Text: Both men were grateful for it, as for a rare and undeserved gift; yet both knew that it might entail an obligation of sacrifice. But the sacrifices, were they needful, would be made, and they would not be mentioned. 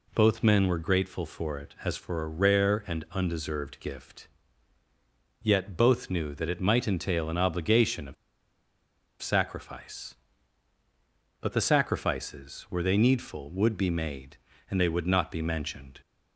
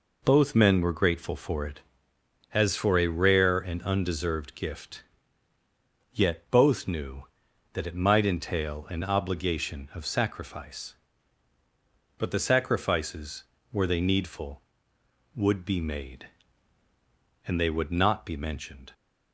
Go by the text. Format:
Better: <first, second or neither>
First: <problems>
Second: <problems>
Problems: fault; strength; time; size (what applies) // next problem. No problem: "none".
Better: second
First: pauses between "of" and "sacrifice"; at 8.1 s; 1.0 s long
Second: none